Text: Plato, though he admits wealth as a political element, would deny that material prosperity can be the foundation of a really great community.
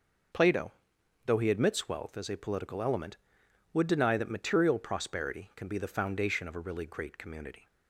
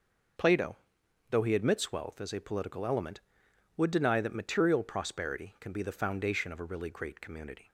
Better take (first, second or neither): neither